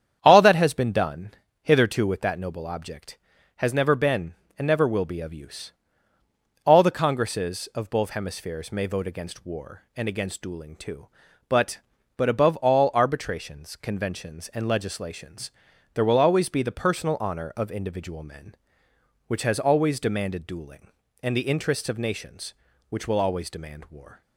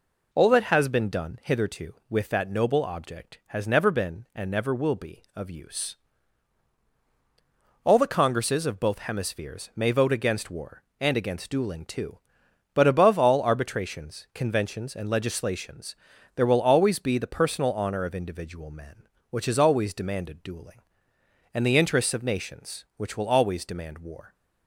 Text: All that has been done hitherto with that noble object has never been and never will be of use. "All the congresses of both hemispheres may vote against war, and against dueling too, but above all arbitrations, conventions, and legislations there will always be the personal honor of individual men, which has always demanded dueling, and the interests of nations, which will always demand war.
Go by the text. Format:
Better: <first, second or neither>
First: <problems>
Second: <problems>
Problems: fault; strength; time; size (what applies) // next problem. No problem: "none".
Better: second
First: starts louder than the rest; strong; until 1.2 s; 8.5 dB // pauses between "done" and "hitherto"; slight; at 1.3 s; 0.32 s long // says "but" twice; at 12.1 s // pauses between "legislations" and "there"; at 15.5 s; 0.42 s long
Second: pauses between "legislations" and "there"; at 15.9 s; 0.38 s long